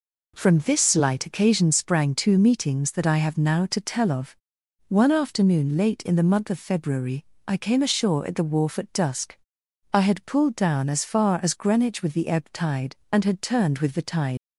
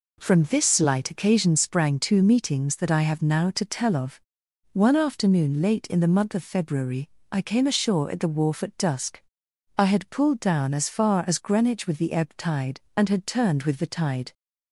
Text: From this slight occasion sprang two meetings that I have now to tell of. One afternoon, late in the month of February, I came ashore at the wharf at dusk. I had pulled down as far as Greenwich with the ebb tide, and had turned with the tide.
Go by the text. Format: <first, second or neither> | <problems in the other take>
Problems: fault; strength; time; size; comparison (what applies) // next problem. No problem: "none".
second | leaves "tide" unfinished; at 14.3 s; 110 ms